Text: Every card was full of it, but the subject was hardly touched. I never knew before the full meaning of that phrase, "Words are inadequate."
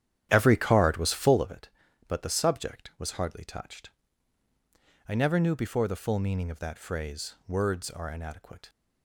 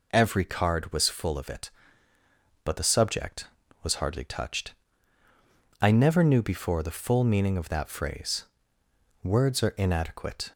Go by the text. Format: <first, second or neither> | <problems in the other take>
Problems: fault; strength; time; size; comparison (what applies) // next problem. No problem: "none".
second | starts louder than the rest; strong; until 1.6 s; 10.5 dB